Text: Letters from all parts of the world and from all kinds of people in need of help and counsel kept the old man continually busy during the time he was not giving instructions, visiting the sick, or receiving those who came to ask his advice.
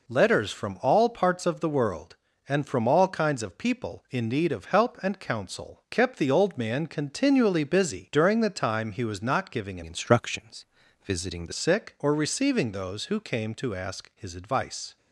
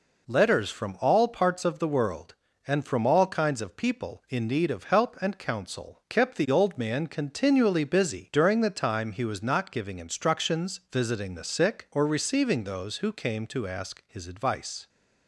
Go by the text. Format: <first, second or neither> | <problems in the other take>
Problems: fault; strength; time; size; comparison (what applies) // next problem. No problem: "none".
second | changes voice from "instructions" to "the"; from 9.8 to 11.5 s; 1.7 s long